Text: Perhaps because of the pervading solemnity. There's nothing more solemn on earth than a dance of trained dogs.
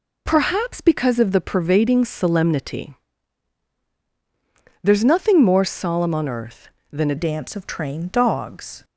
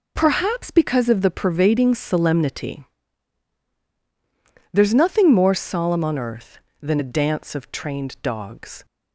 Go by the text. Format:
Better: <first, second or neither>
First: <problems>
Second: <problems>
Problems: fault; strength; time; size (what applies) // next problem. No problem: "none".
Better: second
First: changes voice at "dance"; from 7.1 s on; 1.7 s long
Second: none